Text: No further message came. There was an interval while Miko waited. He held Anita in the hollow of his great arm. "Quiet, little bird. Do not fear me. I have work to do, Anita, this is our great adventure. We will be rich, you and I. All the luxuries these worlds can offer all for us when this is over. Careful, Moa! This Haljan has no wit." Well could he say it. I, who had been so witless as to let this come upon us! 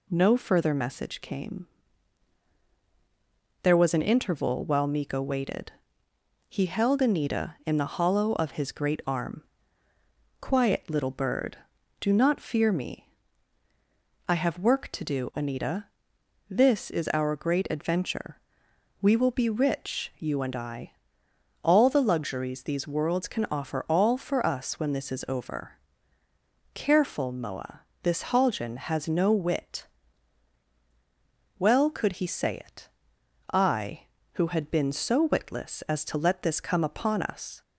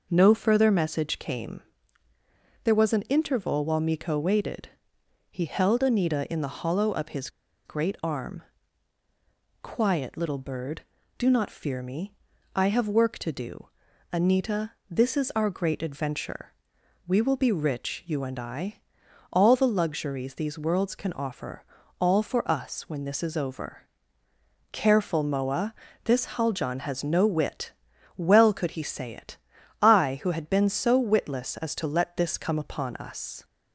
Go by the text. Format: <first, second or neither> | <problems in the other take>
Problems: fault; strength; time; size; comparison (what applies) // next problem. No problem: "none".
first | pauses between "his" and "great"; at 7.2 s; 0.37 s long // pauses between "offer" and "all"; slight; at 21.6 s; 0.34 s long